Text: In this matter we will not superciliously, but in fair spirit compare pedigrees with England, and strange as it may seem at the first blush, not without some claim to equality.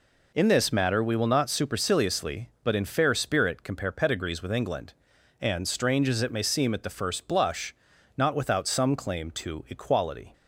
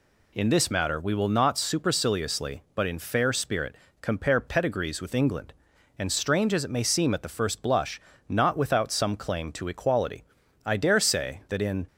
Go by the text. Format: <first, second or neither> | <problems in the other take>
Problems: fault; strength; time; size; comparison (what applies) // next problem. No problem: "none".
first | pauses between "spirit" and "compare"; slight; at 3.7 s; 0.26 s long // goes on to say "I dare say that in"; noticeable; from 10.6 s on; 1.2 s long